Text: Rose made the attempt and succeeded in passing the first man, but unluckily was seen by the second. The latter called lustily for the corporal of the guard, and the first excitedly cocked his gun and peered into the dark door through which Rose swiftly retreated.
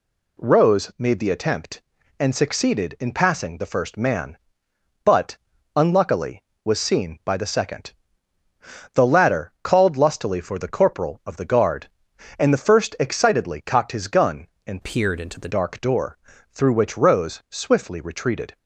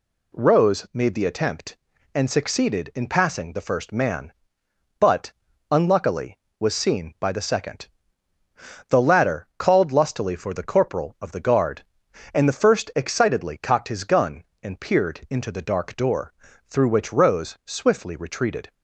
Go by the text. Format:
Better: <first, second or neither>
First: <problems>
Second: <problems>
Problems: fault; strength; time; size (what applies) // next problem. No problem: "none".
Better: second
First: pauses between "but" and "unluckily"; at 5.3 s; 0.38 s long // changes voice from "peered" to "the"; from 14.8 to 15.4 s; 0.6 s long // pauses between "door" and "through"; slight; at 16.1 s; 0.34 s long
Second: pauses between "but" and "unluckily"; at 5.3 s; 0.38 s long // pauses between "door" and "through"; slight; at 16.3 s; 0.34 s long